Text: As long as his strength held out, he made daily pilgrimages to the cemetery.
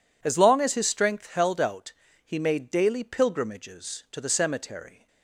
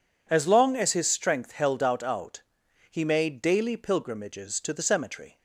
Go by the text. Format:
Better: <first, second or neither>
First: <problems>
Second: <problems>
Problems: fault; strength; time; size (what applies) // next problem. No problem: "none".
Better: first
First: none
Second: says "out" twice; at 2.0 s